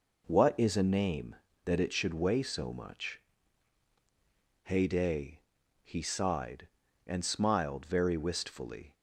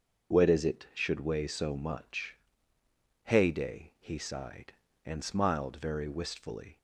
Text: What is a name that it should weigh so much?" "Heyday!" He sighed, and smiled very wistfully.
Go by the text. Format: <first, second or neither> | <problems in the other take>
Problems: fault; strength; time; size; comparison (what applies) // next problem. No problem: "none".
first | starts louder than the rest; until 1.4 s; 6.5 dB // skips "a name that"; at 0.6 s